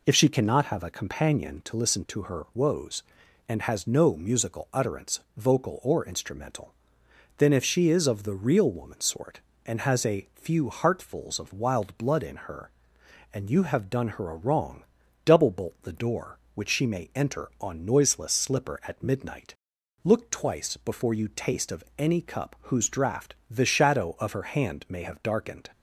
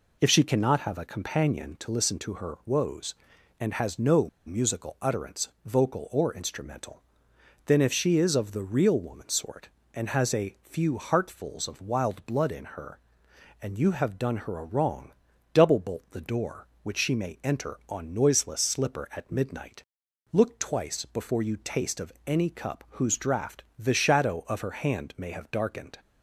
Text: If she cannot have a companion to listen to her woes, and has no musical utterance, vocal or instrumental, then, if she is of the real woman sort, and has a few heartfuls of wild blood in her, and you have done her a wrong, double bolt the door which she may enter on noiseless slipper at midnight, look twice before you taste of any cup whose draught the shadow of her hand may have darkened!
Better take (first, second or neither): first